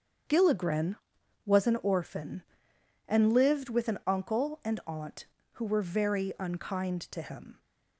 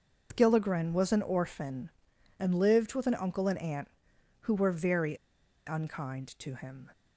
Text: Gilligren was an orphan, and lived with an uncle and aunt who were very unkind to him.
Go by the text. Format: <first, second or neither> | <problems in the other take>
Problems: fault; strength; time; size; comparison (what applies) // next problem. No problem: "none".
first | starts louder than the rest; noticeable; until 1.3 s; 6 dB; strong in the first // pauses between "very" and "unkind"; noticeable; at 5.1 s; 0.49 s long